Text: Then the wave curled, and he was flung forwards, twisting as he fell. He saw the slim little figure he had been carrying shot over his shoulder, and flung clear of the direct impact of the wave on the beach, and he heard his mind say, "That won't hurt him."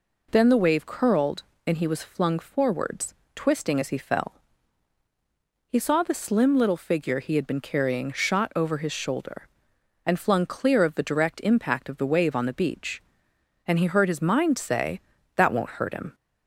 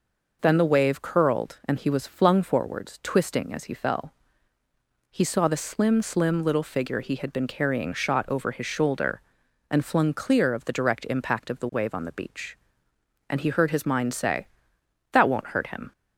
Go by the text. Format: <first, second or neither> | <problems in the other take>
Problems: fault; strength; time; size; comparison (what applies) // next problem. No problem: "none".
first | says "slim" twice; at 6.0 s